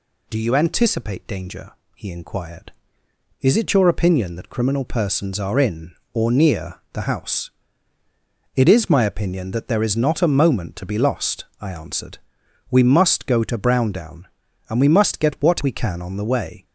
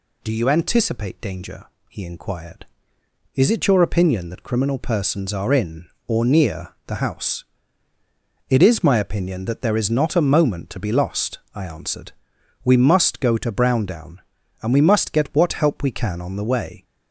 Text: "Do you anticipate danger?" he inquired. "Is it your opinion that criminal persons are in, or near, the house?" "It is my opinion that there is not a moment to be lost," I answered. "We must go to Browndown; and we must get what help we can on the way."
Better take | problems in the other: second | skips "help"; at 15.6 s

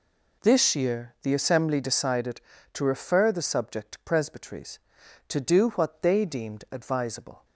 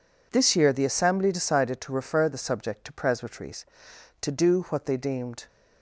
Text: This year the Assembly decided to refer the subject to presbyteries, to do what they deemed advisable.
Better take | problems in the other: first | stops before "advisable"; at 5.4 s

